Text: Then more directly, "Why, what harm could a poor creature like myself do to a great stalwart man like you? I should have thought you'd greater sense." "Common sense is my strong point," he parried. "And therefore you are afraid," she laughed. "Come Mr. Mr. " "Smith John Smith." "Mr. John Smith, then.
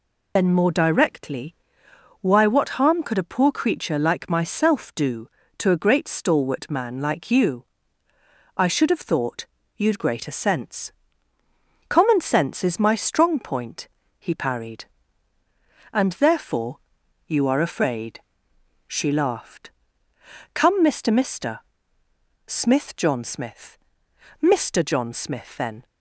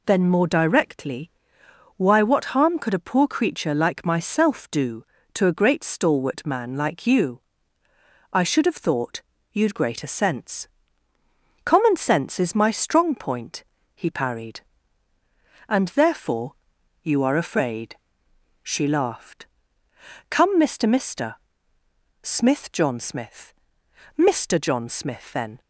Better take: second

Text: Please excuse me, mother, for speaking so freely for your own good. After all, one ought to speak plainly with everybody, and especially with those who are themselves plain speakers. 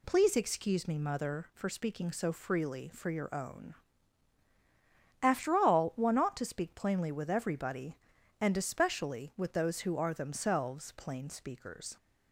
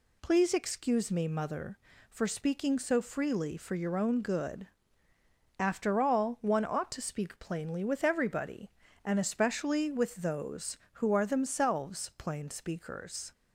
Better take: second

